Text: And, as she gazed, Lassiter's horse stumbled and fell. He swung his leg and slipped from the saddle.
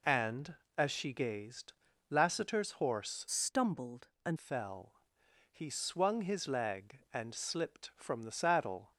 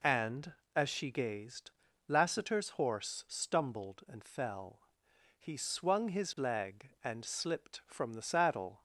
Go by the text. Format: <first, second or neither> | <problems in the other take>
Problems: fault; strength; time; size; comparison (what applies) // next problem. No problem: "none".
second | changes voice from "stumbled" to "and"; from 3.3 to 4.3 s; 1.0 s long